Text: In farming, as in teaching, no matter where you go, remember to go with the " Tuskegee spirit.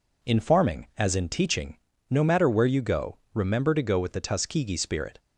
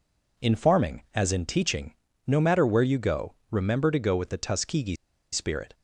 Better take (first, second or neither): first